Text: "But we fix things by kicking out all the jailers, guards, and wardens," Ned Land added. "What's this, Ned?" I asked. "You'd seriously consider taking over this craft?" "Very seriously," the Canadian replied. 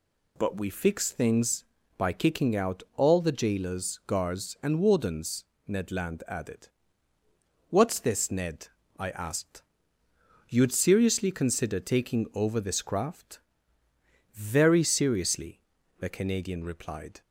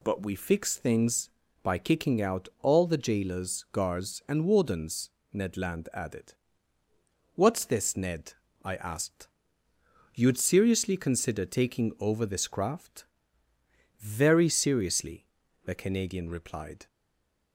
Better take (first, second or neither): first